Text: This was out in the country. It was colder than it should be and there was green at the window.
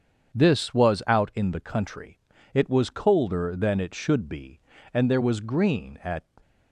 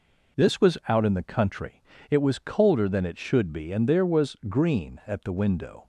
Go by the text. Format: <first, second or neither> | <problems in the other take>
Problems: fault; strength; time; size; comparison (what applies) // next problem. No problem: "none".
second | starts louder than the rest; strong; until 1.4 s; 7.5 dB // stops before "the window"; at 6.4 s